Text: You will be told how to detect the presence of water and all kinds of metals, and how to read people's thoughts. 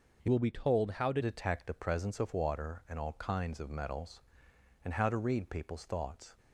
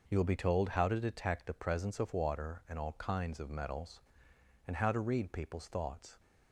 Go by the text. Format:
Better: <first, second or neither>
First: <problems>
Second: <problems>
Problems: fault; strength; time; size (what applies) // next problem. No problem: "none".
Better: second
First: changes voice from "will" to "to"; from 0.3 to 1.2 s; 0.9 s long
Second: none